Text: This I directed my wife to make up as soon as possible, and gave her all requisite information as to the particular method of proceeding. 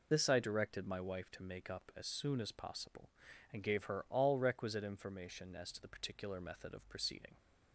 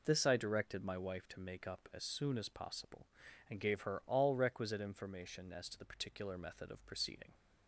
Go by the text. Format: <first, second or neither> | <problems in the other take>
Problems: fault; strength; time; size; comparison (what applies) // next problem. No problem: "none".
second | loses the start of "This"; at 0.1 s; 30 ms